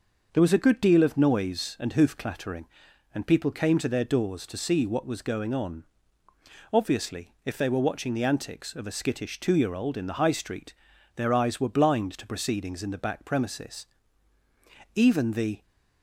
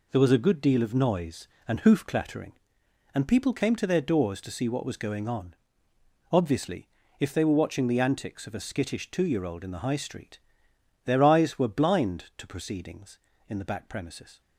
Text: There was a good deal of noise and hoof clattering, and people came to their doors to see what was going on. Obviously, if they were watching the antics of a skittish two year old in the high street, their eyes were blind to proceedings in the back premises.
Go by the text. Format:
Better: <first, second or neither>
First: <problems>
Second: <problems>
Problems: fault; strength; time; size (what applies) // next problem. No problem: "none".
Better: second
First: starts louder than the rest; noticeable; until 1.3 s; 6 dB // goes on to say "Even the"; noticeable; from 14.9 s on; 0.68 s long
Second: none